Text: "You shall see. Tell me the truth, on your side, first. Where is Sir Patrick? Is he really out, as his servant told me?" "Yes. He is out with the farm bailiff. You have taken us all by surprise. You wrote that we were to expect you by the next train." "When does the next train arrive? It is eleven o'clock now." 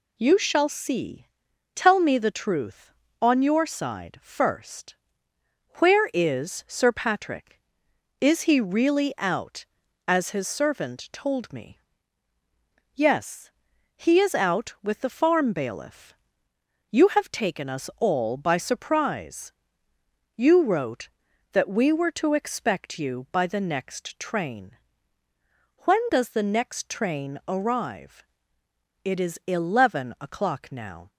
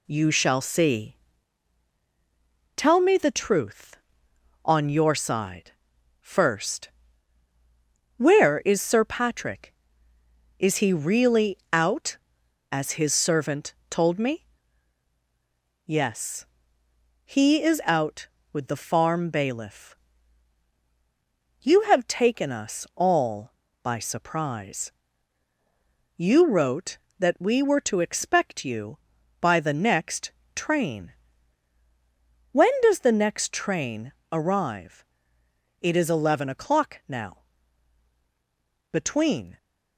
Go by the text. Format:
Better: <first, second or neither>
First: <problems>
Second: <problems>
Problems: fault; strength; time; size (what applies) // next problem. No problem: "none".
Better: first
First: none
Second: pauses between "really" and "out"; slight; at 11.5 s; 0.16 s long // pauses between "servant" and "told"; slight; at 13.7 s; 0.16 s long // pauses between "next" and "train"; slight; at 30.3 s; 0.24 s long // pauses between "train" and "arrive"; slight; at 34.1 s; 0.18 s long // goes on to say "Between"; noticeable; from 38.9 s on; 0.66 s long